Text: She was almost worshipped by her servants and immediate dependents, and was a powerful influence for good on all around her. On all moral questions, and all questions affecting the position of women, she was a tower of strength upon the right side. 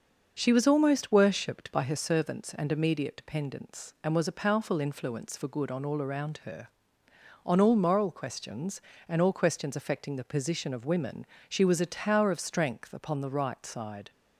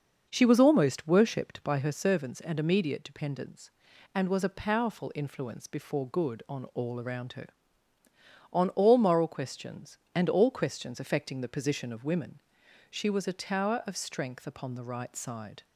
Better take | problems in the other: first | starts louder than the rest; noticeable; until 1.3 s; 6 dB; noticeable in the first // says "before" for "for"; at 5.6 s

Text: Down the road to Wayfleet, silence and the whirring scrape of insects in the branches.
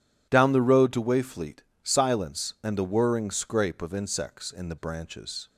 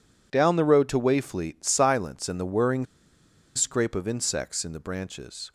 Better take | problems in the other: first | pauses between "whirring" and "scrape"; noticeable; at 2.8 s; 0.71 s long

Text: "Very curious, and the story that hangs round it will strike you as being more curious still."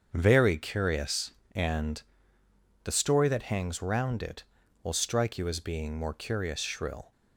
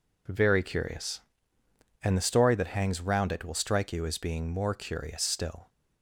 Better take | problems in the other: second | starts louder than the rest; until 1.1 s; 7 dB // pauses between "and" and "the"; noticeable; at 2.0 s; 0.82 s long // says "shrill" for "still"; at 6.6 s

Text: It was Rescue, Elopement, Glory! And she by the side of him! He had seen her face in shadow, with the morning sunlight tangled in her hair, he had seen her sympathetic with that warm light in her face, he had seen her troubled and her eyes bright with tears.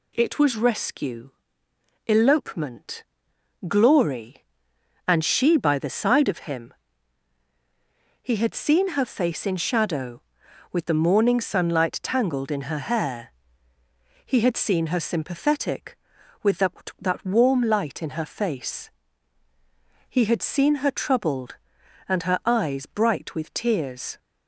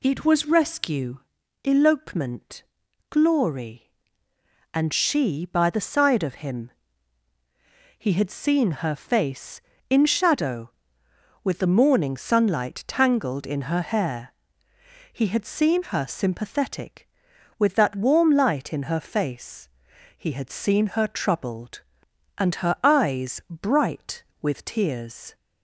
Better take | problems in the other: second | says "that" twice; at 17.0 s

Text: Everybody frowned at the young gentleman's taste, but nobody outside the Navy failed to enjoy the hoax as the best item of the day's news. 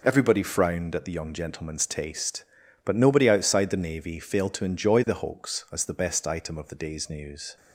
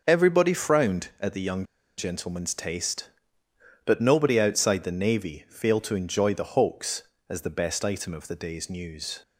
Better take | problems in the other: first | pauses between "young" and "gentleman's"; slight; at 1.6 s; 0.34 s long

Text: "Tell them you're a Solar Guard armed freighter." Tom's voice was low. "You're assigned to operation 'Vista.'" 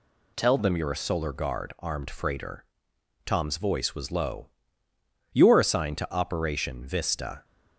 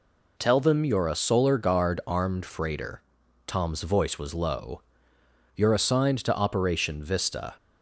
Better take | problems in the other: second | changes voice at "them"; from 0.5 s on; 6.9 s long

